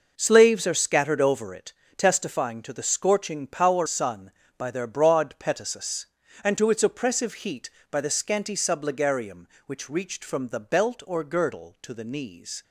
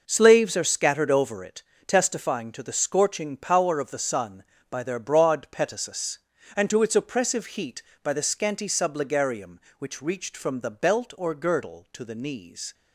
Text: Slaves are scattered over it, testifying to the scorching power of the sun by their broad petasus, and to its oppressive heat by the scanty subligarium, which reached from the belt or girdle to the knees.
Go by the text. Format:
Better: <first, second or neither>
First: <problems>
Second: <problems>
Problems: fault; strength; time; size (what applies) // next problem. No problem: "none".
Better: second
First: skips "of the"; at 3.8 s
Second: none